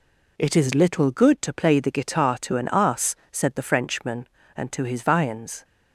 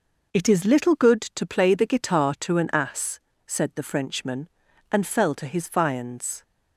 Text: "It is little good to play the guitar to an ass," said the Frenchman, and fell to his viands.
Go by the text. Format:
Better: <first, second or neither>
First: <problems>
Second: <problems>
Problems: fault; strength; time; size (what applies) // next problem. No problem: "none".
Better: second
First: skips "fell"; at 4.7 s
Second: none